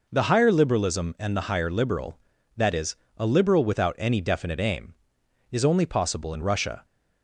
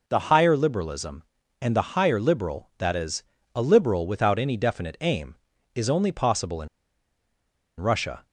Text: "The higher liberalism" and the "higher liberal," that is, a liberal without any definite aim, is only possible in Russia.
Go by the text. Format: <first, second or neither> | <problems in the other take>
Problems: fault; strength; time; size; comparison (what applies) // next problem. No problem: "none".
first | pauses between "in" and "Russia"; at 6.6 s; 1.1 s long